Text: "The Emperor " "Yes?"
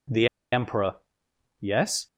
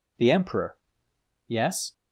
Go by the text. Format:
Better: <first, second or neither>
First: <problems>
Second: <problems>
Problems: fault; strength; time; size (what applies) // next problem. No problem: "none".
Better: second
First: pauses between "The" and "Emperor"; slight; at 0.2 s; 0.25 s long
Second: none